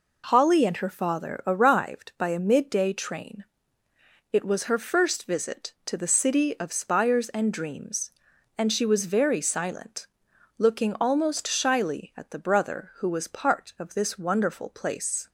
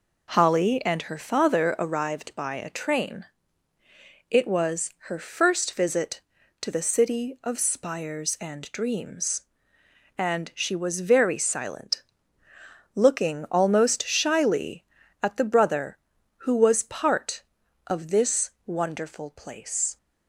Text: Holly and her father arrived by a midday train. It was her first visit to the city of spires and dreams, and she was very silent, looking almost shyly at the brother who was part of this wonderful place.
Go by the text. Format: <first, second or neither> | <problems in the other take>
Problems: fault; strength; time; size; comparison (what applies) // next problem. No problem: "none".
first | skips "midday"; at 2.6 s // pauses between "was" and "her"; slight; at 4.9 s; 0.16 s long // pauses between "this" and "wonderful"; slight; at 18.5 s; 0.16 s long